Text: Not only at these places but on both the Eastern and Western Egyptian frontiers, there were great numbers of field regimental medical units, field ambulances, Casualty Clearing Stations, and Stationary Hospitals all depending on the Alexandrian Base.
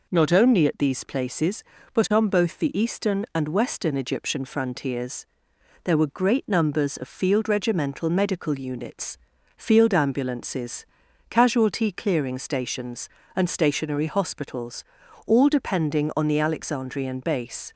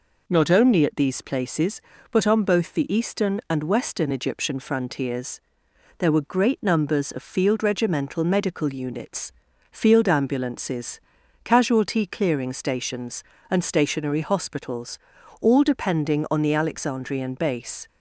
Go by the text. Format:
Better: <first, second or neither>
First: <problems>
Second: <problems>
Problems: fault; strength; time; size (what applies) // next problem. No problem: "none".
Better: neither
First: pauses between "Hospitals" and "all"; at 14.8 s; 0.42 s long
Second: pauses between "Hospitals" and "all"; at 14.9 s; 0.42 s long